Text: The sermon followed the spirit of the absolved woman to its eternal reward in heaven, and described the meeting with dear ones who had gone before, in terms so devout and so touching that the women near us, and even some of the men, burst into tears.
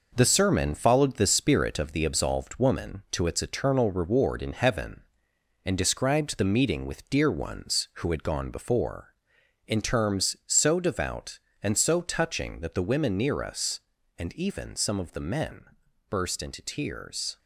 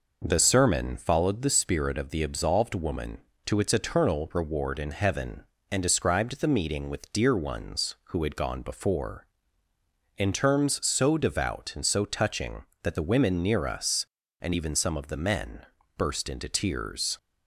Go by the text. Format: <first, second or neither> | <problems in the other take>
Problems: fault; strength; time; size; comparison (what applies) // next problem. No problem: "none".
second | gets quieter; noticeable; throughout; 6 dB